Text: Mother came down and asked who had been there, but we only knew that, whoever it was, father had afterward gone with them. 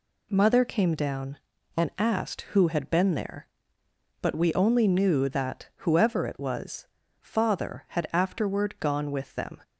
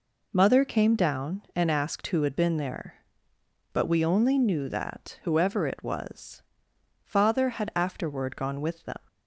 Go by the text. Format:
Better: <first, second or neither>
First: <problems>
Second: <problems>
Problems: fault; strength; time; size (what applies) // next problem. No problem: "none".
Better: neither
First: none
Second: none